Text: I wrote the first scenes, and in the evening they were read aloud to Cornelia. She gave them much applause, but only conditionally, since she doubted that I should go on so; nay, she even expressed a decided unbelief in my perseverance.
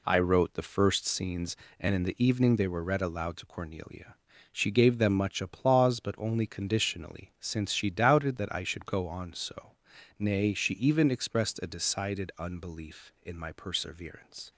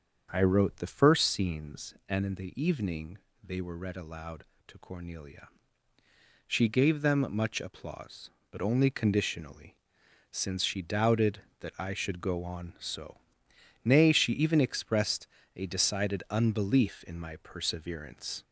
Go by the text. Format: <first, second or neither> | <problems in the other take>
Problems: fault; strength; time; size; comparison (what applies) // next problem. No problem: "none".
first | gets louder; slight; throughout; 2.5 dB // starts louder than the rest; until 1.3 s; 7 dB // pauses between "evening" and "they"; slight; at 3.1 s; 0.26 s long // pauses between "expressed" and "a"; slight; at 15.2 s; 0.30 s long